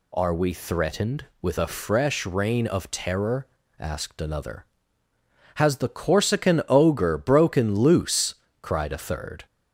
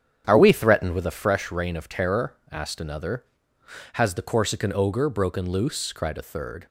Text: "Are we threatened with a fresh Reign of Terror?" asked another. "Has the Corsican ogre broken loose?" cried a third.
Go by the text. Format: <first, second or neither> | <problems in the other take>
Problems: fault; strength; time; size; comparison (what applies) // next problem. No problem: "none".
first | starts louder than the rest; strong; until 1.3 s; 8.5 dB